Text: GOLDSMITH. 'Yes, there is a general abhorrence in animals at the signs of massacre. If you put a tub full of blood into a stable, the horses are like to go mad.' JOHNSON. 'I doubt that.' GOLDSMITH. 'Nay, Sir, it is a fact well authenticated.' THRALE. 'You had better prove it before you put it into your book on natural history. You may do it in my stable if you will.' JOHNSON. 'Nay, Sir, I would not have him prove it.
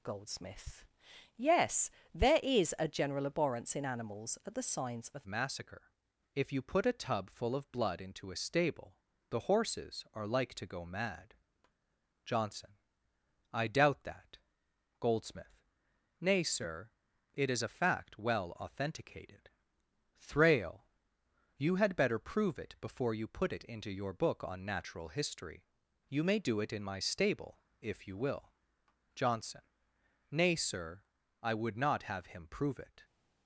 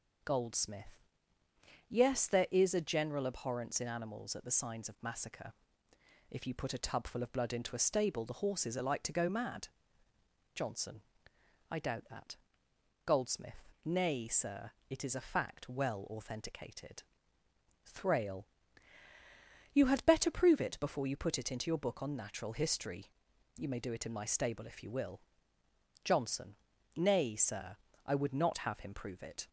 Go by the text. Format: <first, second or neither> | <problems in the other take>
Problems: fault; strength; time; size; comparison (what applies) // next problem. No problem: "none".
second | changes voice at "massacre"; from 5.2 s on; 27.8 s long // pauses between "stable" and "if"; slight; at 27.6 s; 0.18 s long